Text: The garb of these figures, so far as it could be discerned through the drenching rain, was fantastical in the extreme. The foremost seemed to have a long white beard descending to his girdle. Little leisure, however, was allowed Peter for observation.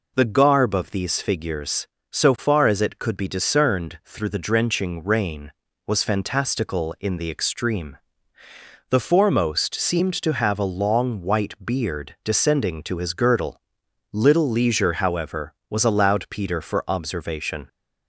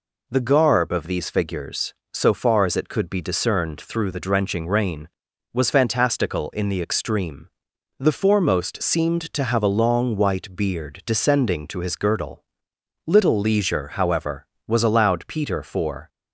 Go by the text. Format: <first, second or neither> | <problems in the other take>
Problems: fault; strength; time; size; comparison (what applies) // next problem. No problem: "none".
first | stops before "observation"; at 16.0 s